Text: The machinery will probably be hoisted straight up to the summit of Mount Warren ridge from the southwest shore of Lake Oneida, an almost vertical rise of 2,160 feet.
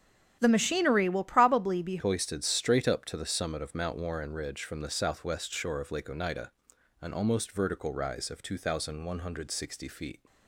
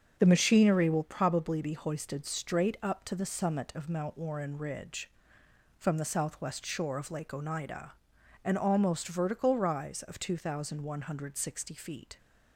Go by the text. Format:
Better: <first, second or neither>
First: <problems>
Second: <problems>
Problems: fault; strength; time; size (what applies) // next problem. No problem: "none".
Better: second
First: starts louder than the rest; strong; until 1.4 s; 9 dB // changes voice at "hoisted"; from 1.9 s on; 8.2 s long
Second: starts louder than the rest; until 1.1 s; 7 dB